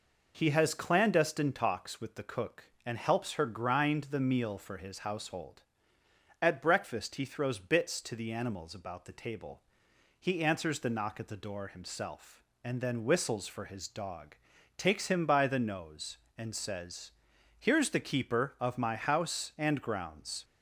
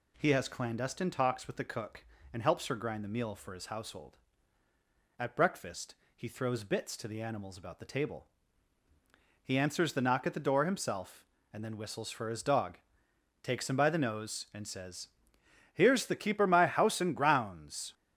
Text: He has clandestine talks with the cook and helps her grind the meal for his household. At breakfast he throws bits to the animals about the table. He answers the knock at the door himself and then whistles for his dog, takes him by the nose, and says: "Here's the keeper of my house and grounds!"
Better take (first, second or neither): first